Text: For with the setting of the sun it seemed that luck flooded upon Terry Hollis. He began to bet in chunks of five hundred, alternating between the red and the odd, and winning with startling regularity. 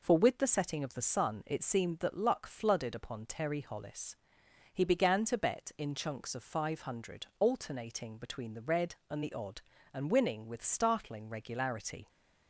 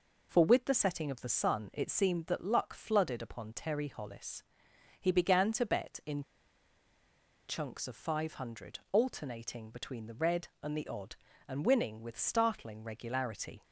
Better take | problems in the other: first | pauses between "in" and "chunks"; strong; at 6.2 s; 1.2 s long

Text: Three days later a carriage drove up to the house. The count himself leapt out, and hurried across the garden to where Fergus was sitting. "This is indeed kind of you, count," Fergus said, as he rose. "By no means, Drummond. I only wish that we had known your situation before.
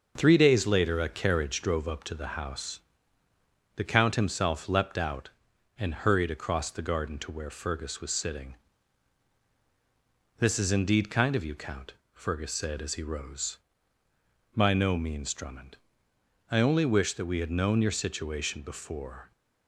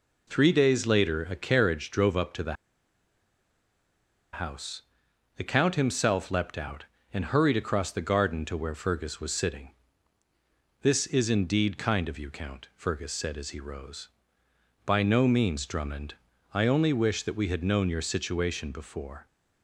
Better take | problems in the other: first | pauses between "the" and "house"; strong; at 2.5 s; 1.7 s long

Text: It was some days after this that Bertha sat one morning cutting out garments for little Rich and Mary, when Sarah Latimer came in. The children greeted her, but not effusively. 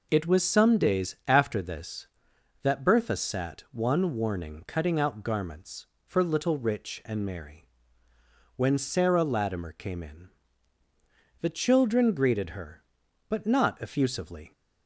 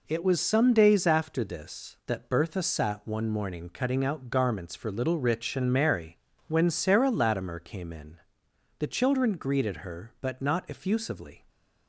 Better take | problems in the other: second | says "warning" for "morning"; at 4.1 s

